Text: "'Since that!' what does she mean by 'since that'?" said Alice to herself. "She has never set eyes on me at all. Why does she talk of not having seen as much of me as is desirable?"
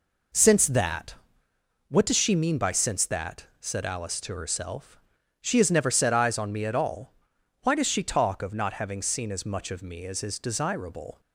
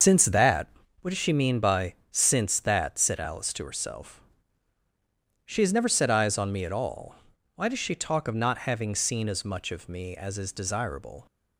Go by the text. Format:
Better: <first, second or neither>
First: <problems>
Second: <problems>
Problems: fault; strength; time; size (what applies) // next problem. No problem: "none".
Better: first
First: none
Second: loses the start of "Since"; at 0.0 s; 95 ms // starts louder than the rest; until 1.3 s; 6.5 dB // pauses between "by" and "since"; slight; at 1.9 s; 0.16 s long